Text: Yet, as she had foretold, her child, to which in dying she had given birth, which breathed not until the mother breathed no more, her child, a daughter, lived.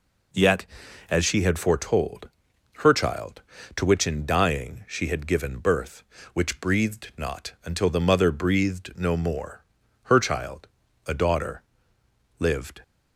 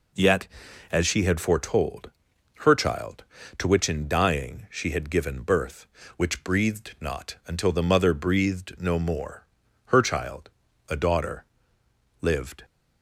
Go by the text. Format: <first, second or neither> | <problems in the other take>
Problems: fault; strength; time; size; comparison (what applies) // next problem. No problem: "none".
neither | none